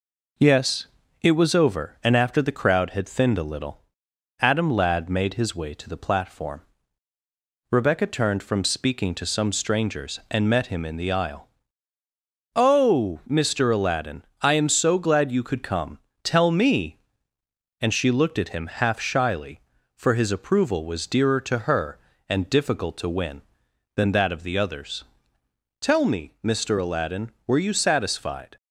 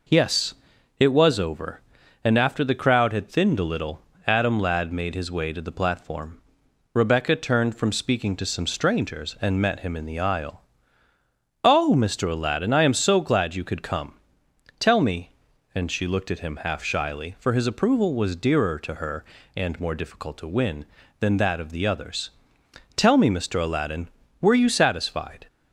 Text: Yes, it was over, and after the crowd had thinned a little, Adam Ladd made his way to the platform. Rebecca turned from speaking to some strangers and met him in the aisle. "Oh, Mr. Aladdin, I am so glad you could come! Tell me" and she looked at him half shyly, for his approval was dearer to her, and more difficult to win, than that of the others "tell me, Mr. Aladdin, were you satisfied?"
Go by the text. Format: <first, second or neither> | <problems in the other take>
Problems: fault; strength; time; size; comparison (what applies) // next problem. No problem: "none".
second | skips "more"; at 22.4 s // pauses between "others" and "tell"; noticeable; at 25.0 s; 0.74 s long; noticeable in the second